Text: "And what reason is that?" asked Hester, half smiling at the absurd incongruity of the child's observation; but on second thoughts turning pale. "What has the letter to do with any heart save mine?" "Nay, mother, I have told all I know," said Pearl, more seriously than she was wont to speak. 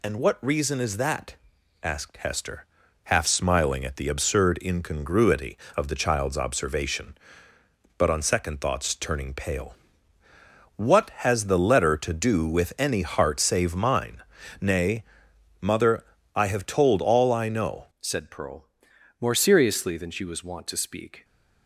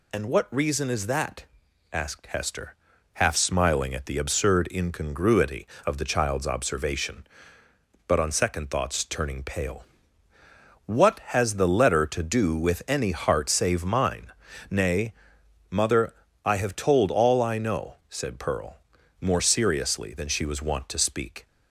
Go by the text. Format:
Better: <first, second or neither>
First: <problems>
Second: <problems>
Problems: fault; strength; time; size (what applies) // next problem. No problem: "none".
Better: second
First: changes voice at "said"; from 18.0 s on; 3.2 s long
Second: none